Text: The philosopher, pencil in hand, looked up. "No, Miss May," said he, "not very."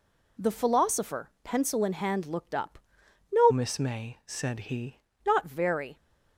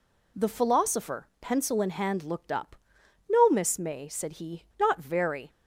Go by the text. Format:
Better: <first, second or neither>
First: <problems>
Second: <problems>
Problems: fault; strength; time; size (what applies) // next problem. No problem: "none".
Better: second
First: changes voice from "Miss" to "he"; from 3.5 to 5.0 s; 1.5 s long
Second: none